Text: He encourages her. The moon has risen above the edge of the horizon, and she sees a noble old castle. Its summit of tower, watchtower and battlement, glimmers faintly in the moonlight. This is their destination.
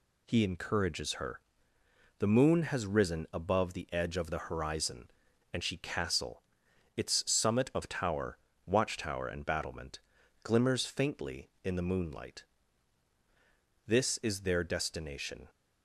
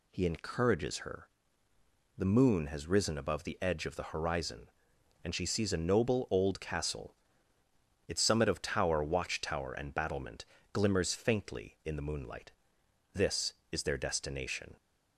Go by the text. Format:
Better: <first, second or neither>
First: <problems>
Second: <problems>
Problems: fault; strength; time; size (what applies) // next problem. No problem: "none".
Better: second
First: skips "sees a noble old"; at 5.7 s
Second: none